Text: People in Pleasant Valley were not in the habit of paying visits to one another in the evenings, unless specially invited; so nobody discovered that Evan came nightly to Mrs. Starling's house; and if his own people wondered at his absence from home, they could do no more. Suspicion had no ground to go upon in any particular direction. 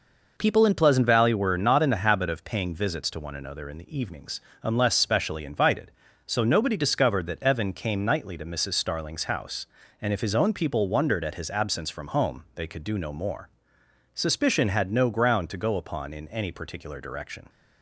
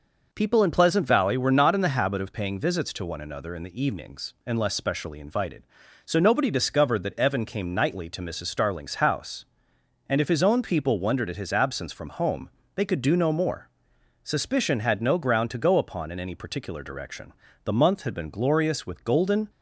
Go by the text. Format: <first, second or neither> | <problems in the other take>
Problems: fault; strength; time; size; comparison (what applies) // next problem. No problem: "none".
first | goes on to say "The month had been glorious with golden"; strong; from 17.6 s on; 1.8 s long